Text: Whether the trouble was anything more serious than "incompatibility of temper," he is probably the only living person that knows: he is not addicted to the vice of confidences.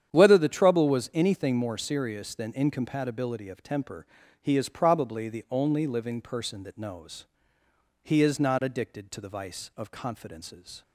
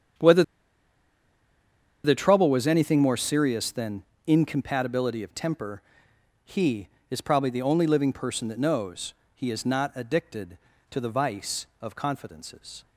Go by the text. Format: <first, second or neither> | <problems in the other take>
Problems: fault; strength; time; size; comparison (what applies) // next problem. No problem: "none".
first | starts louder than the rest; strong; until 2.8 s; 8.5 dB; strong in the first // pauses between "Whether" and "the"; strong; at 0.4 s; 1.6 s long // pauses between "than" and "incompatibility"; slight; at 4.0 s; 0.22 s long